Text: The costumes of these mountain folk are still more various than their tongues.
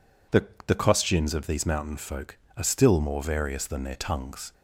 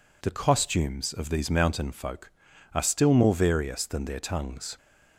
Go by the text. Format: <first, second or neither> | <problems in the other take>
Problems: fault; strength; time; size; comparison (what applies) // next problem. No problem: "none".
second | says "The" twice; at 0.6 s